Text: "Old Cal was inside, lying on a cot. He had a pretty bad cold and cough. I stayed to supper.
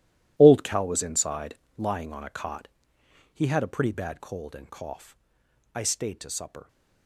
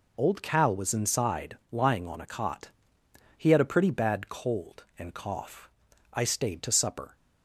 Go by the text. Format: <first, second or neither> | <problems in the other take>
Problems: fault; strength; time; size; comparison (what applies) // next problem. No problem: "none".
second | gets quieter; strong; throughout; 14.5 dB